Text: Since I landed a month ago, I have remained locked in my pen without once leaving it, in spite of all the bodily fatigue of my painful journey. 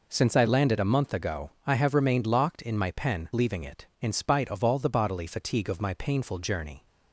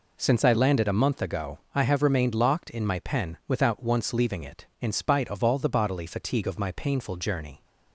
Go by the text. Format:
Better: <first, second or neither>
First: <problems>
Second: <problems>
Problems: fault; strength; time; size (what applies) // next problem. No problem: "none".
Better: second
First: skips "without once"; at 3.3 s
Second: none